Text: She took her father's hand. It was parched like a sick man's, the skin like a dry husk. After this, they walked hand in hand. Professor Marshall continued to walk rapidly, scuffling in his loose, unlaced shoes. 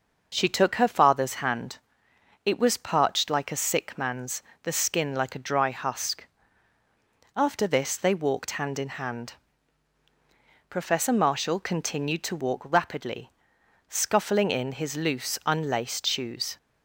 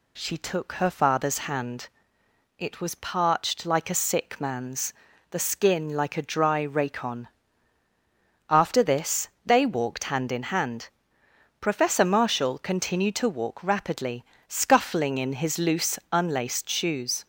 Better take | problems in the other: first | says "racon" for "husk"; at 6.6 s

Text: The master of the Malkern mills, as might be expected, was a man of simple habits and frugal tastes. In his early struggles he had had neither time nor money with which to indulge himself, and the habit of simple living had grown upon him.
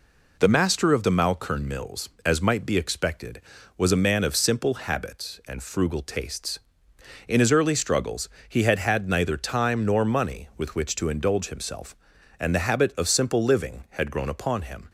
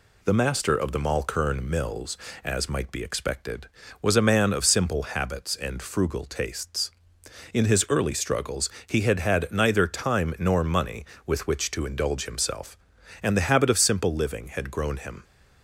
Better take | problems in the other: first | pauses between "struggles" and "he"; slight; at 8.6 s; 0.18 s long; slight in the first // skips "upon"; at 14.9 s

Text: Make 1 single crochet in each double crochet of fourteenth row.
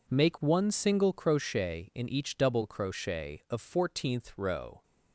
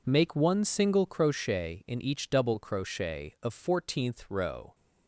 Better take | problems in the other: neither | none

